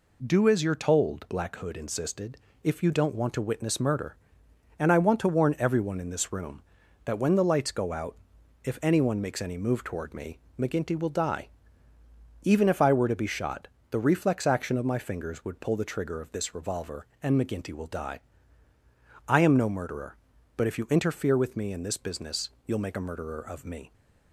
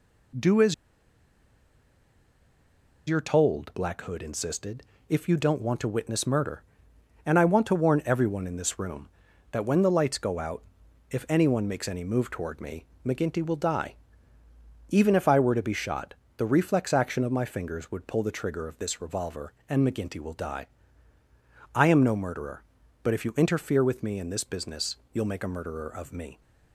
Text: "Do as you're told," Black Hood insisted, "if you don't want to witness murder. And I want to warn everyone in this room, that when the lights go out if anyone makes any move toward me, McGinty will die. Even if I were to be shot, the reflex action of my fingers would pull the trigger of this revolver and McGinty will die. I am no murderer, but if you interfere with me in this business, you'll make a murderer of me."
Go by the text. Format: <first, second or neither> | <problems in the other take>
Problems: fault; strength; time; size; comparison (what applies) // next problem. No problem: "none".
first | pauses between "as" and "you're"; strong; at 0.7 s; 2.3 s long // pauses between "out" and "if"; noticeable; at 10.6 s; 0.46 s long; noticeable in the first